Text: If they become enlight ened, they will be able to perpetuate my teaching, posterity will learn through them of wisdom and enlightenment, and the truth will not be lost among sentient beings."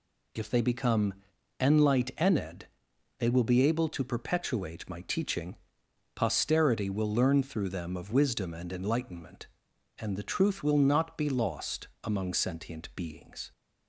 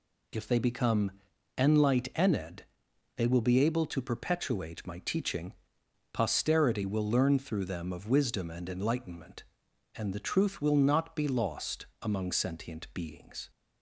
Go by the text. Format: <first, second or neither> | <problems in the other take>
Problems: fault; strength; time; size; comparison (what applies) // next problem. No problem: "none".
neither | pauses between "become" and "enlight"; noticeable; the same in both // pauses between "lost" and "among"; slight; the same in both